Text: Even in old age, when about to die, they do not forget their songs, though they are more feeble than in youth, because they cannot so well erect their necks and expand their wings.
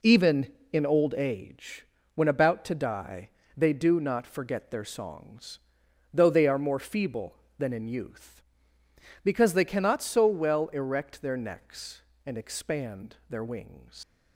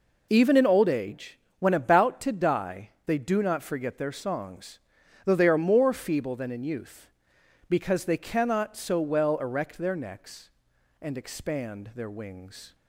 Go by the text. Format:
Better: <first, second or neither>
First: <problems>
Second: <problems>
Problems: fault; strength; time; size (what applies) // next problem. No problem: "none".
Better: second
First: leaves "wings" unfinished; at 14.0 s; 115 ms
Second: none